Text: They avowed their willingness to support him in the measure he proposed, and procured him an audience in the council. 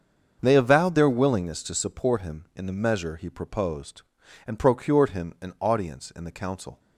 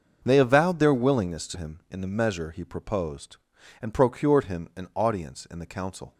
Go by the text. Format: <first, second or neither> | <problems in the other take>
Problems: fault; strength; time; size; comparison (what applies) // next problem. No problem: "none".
first | starts louder than the rest; noticeable; until 1.2 s; 6 dB; also in the first // skips "support"; at 1.5 s